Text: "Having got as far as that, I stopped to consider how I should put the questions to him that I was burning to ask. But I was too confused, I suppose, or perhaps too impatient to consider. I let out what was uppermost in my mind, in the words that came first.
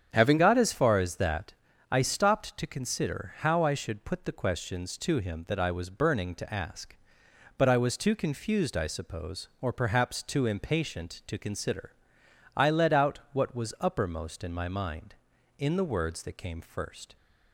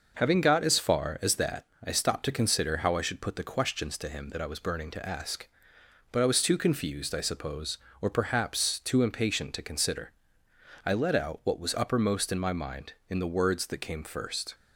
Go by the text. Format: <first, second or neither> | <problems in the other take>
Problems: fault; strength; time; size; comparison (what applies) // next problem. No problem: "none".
second | starts louder than the rest; strong; until 1.1 s; 8.5 dB // changes voice at "got"; from 0.3 s on; 16.8 s long